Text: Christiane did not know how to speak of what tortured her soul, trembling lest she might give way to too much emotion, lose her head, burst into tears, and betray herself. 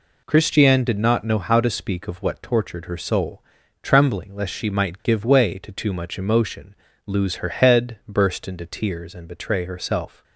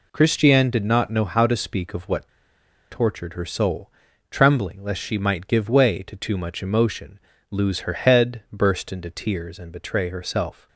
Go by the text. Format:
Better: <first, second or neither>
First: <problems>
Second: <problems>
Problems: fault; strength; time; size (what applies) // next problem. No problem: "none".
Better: first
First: none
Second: pauses between "what" and "tortured"; noticeable; at 2.2 s; 0.63 s long